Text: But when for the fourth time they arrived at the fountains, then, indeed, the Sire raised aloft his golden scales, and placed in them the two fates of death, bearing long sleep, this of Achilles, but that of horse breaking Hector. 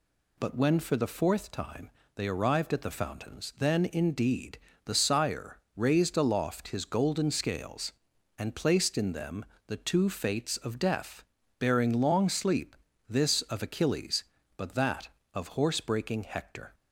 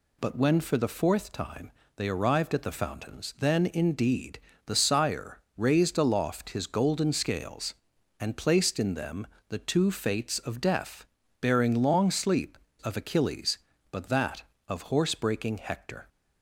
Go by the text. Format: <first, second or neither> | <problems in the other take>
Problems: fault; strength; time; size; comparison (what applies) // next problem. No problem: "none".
first | pauses between "time" and "they"; slight; at 1.7 s; 0.24 s long; slight in the first // pauses between "Sire" and "raised"; slight; at 5.3 s; 0.16 s long; slight in the first // pauses between "them" and "the"; slight; at 9.2 s; 0.22 s long; slight in the first // skips "this"; at 12.6 s